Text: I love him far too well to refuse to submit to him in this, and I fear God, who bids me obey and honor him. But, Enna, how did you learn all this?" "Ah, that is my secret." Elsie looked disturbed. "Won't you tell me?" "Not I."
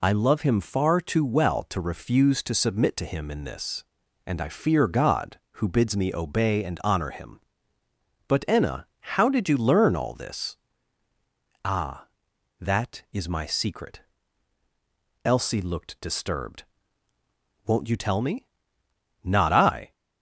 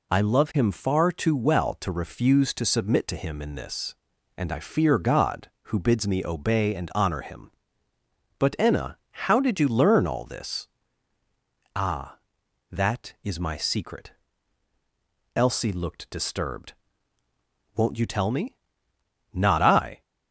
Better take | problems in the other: neither | none

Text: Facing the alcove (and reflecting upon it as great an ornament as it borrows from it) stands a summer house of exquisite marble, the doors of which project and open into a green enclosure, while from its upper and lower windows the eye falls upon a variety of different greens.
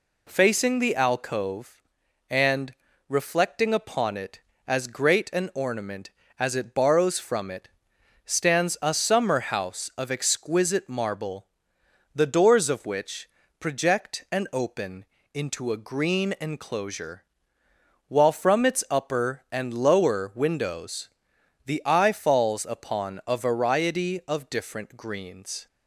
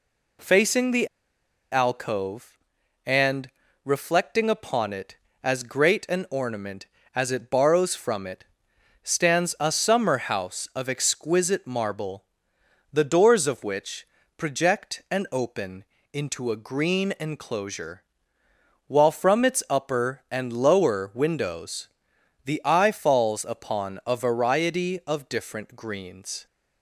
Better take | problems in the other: first | pauses between "the" and "alcove"; noticeable; at 1.0 s; 0.65 s long // pauses between "and" and "reflecting"; slight; at 3.4 s; 0.34 s long; slight in the first // pauses between "which" and "project"; slight; at 14.0 s; 0.32 s long; slight in the first // pauses between "open" and "into"; slight; at 15.8 s; 0.30 s long; slight in the first // pauses between "windows" and "the"; noticeable; at 21.8 s; 0.56 s long; noticeable in the first

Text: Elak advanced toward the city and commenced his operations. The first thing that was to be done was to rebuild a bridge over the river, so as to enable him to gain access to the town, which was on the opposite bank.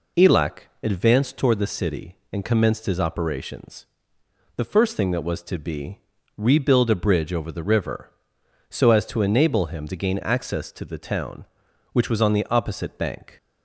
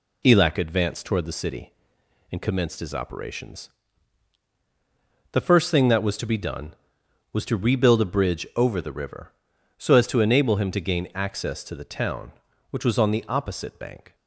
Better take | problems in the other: second | pauses between "Elak" and "advanced"; slight; at 0.6 s; 0.20 s long // skips "done was to"; at 6.1 s

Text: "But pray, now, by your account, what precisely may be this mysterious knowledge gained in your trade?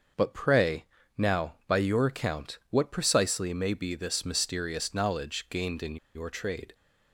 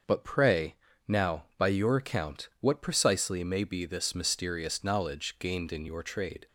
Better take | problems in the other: second | starts louder than the rest; until 1.4 s; 6.5 dB; also in the second // pauses between "in" and "your"; slight; at 5.9 s; 0.19 s long

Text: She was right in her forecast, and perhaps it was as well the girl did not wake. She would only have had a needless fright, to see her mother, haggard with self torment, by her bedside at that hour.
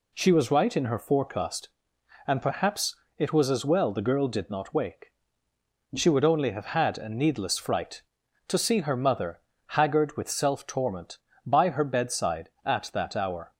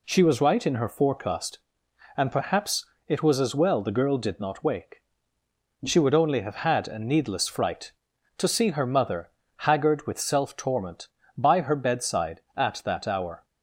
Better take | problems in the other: neither | pauses between "perhaps" and "it"; slight; the same in both

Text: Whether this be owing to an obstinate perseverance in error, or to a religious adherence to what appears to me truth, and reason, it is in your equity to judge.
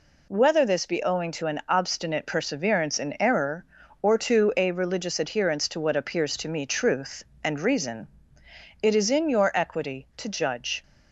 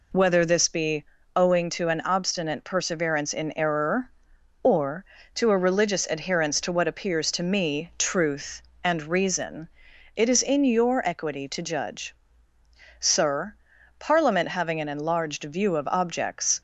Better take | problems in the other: first | pauses between "be" and "owing"; slight; at 1.0 s; 0.28 s long // goes on to say "Sir Parliament having an enlarged view of objects"; strong; from 13.0 s on; 3.6 s long

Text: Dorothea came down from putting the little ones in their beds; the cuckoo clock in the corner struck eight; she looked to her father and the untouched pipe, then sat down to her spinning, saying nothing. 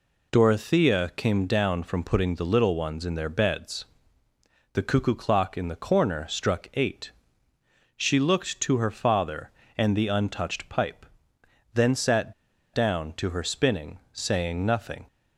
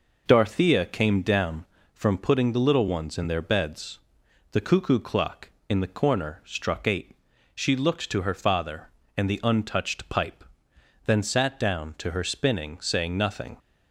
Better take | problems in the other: second | pauses between "sat" and "down"; at 12.3 s; 0.41 s long

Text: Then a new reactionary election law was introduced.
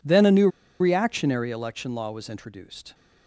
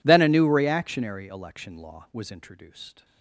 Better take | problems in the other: second | pauses between "new" and "reactionary"; slight; at 0.4 s; 0.31 s long

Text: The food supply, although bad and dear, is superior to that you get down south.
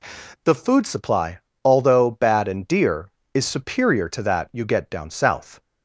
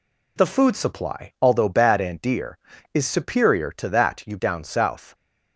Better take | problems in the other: first | skips "get"; at 4.3 s

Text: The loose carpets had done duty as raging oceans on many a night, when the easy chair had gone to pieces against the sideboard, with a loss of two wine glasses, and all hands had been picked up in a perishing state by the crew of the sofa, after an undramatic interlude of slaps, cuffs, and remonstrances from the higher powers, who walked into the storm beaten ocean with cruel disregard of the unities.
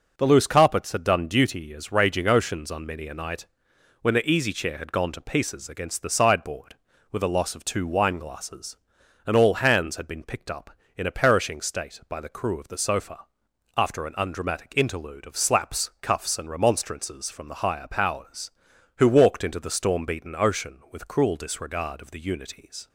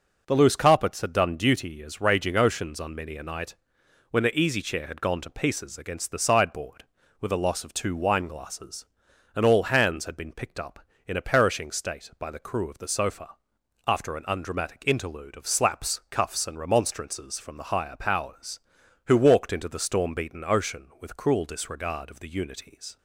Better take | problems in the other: neither | none

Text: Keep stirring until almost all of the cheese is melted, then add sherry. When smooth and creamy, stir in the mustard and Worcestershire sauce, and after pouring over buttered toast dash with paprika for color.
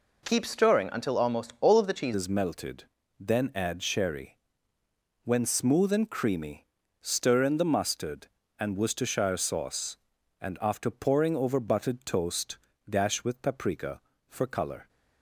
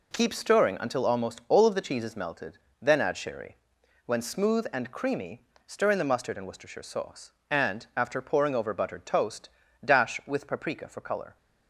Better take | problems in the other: second | changes voice at "is"; from 2.1 s on; 12.7 s long // pauses between "toast" and "dash"; slight; at 12.5 s; 0.30 s long; slight in the second

